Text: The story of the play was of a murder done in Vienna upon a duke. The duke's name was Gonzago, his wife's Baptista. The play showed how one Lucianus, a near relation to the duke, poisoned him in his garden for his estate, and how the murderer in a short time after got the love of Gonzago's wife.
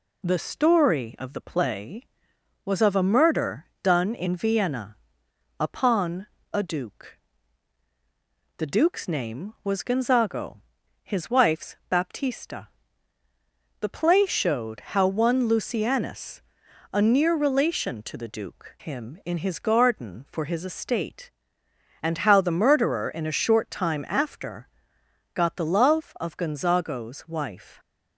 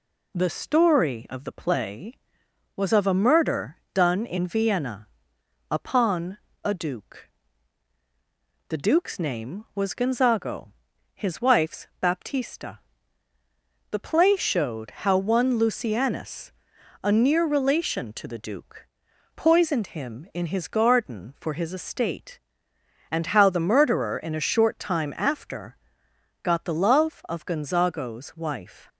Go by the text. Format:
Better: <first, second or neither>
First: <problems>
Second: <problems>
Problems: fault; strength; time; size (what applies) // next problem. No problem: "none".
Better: second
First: pauses between "murder" and "done"; slight; at 3.6 s; 0.16 s long // pauses between "Vienna" and "upon"; noticeable; at 4.9 s; 0.62 s long // pauses between "upon" and "a"; slight; at 6.2 s; 0.24 s long // pauses between "wife's" and "Baptista"; slight; at 11.7 s; 0.16 s long // skips "poisoned"; at 18.7 s // pauses between "after" and "got"; noticeable; at 24.6 s; 0.66 s long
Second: pauses between "murder" and "done"; slight; at 3.7 s; 0.16 s long // pauses between "Vienna" and "upon"; noticeable; at 5.0 s; 0.62 s long // pauses between "upon" and "a"; slight; at 6.3 s; 0.24 s long // pauses between "wife's" and "Baptista"; slight; at 11.8 s; 0.16 s long // pauses between "after" and "got"; noticeable; at 25.7 s; 0.66 s long